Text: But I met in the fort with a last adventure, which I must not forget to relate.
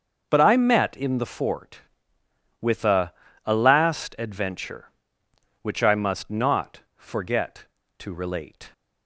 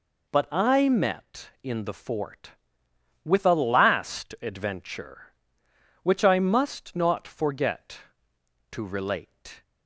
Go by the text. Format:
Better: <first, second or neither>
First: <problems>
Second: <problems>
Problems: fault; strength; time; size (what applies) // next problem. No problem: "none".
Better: second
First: starts louder than the rest; until 1.3 s; 6.5 dB // says "a" twice; at 3.4 s // pauses between "not" and "forget"; slight; at 6.8 s; 0.18 s long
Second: none